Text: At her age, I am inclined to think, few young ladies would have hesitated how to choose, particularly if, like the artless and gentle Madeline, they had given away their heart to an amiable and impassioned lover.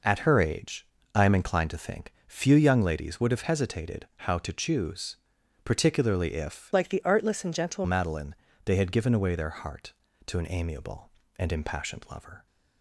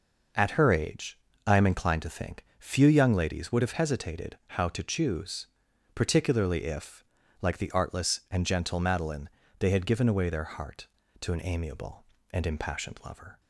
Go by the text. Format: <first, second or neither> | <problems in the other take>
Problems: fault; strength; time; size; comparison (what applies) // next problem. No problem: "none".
second | changes voice from "like" to "gentle"; from 6.7 to 7.8 s; 1.1 s long